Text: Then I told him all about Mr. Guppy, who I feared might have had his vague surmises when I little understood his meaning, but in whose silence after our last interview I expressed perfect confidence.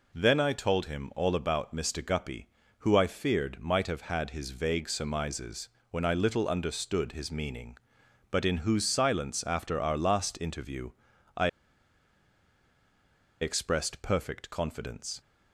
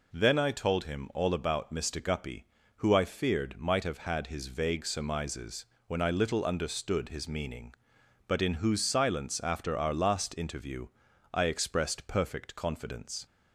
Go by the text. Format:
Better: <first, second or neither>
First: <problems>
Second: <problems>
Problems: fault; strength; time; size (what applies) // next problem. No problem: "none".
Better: second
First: pauses between "surmises" and "when"; slight; at 5.6 s; 0.22 s long // pauses between "interview" and "I"; noticeable; at 10.9 s; 0.46 s long // pauses between "I" and "expressed"; strong; at 11.4 s; 1.9 s long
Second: pauses between "surmises" and "when"; slight; at 5.6 s; 0.22 s long // pauses between "interview" and "I"; noticeable; at 10.8 s; 0.46 s long